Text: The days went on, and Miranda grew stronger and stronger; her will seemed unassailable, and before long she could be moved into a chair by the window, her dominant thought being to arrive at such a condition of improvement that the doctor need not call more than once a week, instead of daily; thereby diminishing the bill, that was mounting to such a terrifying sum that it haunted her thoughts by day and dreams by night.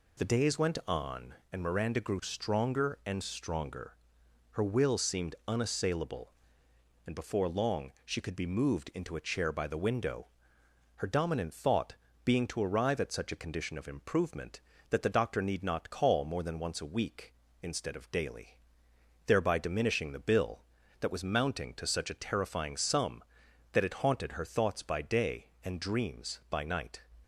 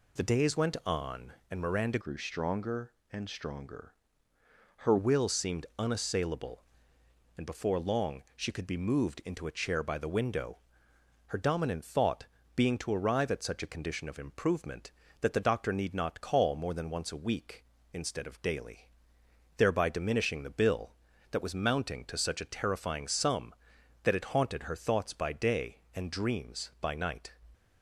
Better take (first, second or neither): first